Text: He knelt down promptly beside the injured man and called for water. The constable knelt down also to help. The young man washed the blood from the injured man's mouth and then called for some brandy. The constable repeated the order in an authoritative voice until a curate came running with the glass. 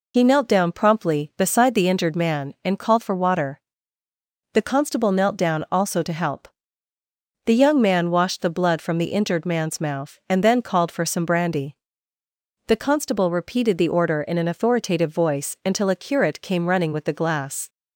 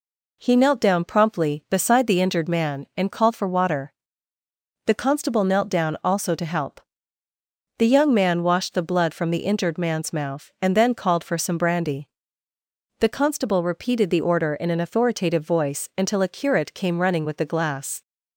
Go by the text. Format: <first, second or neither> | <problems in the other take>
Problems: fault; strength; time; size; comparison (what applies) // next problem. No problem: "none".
second | loses the start of "He"; at 0.1 s; 75 ms